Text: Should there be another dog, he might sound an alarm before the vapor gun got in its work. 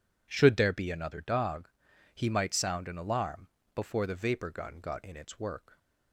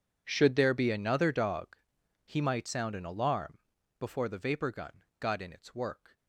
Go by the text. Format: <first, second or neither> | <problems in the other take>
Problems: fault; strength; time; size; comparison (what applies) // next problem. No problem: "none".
first | gets quieter; strong; throughout; 21 dB // pauses between "alarm" and "before"; at 3.5 s; 0.40 s long; slight in the first // pauses between "gun" and "got"; slight; at 5.0 s; 0.16 s long